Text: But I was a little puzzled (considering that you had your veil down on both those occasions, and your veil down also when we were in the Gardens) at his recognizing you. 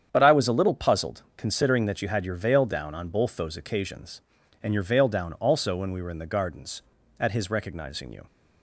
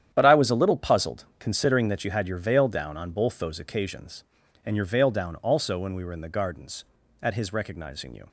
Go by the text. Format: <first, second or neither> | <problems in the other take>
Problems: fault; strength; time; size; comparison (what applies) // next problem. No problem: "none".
first | gets quieter; strong; throughout; 12 dB // starts louder than the rest; strong; until 1.1 s; 9.5 dB; strong in the first